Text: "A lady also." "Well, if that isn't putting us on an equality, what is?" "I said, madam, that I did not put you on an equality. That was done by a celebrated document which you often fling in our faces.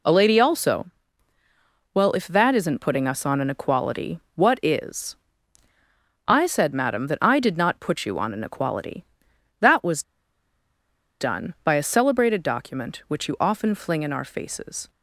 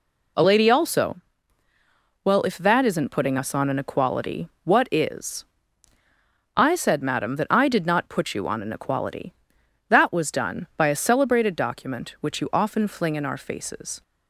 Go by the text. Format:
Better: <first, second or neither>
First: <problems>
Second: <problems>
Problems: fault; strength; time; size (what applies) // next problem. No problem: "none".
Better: second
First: pauses between "was" and "done"; at 10.0 s; 1.1 s long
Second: none